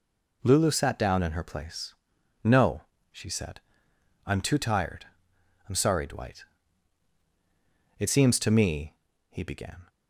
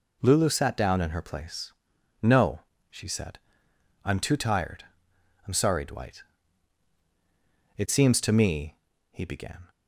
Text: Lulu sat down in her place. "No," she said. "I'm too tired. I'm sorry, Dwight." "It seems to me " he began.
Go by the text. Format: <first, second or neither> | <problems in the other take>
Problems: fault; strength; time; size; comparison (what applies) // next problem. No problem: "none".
neither | none